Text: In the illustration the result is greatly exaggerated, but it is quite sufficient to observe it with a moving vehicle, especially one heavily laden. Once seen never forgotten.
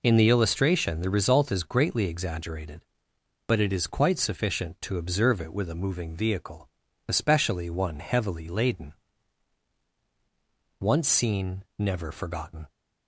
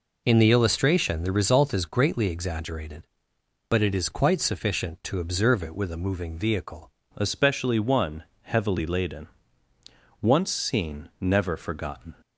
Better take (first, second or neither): first